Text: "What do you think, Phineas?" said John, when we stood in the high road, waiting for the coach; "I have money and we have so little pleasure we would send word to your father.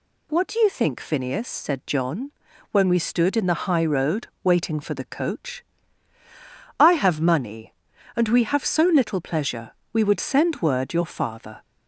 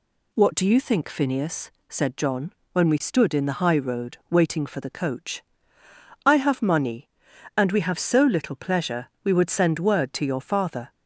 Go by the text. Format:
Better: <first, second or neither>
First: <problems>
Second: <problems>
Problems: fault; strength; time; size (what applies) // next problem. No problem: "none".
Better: second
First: pauses between "pleasure" and "we"; slight; at 9.7 s; 0.20 s long // skips "to"; at 10.9 s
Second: none